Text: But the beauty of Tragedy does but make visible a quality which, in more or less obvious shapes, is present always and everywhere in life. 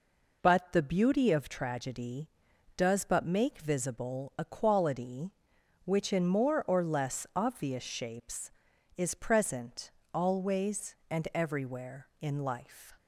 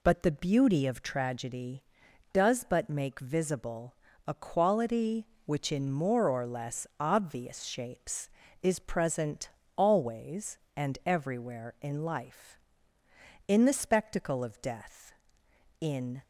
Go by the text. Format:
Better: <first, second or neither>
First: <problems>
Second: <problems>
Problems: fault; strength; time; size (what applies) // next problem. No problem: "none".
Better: first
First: pauses between "present" and "always"; slight; at 9.8 s; 0.24 s long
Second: pauses between "visible" and "a"; slight; at 3.9 s; 0.32 s long // pauses between "present" and "always"; slight; at 9.4 s; 0.28 s long // goes on to say "In the spectacle of Death in"; strong; from 13.4 s on; 2.7 s long